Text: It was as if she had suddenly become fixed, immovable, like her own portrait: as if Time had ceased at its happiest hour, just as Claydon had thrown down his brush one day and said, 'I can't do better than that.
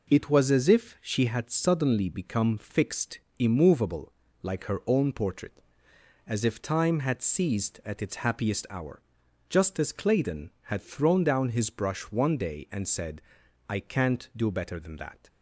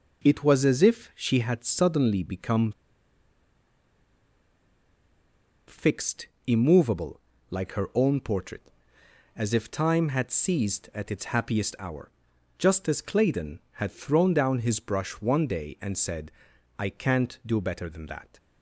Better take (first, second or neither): first